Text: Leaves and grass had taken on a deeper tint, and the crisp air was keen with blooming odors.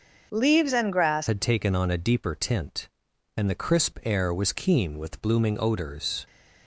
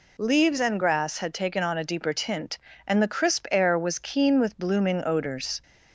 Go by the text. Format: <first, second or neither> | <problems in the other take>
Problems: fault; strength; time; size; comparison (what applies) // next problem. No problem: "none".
second | starts louder than the rest; until 1.3 s; 6.5 dB // changes voice at "had"; from 1.2 s on; 5.0 s long